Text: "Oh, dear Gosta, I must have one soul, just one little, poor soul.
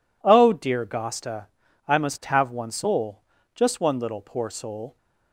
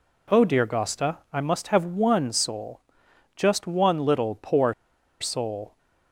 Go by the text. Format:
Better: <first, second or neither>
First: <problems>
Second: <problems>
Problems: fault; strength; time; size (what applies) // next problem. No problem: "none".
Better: first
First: none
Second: pauses between "poor" and "soul"; noticeable; at 4.7 s; 0.47 s long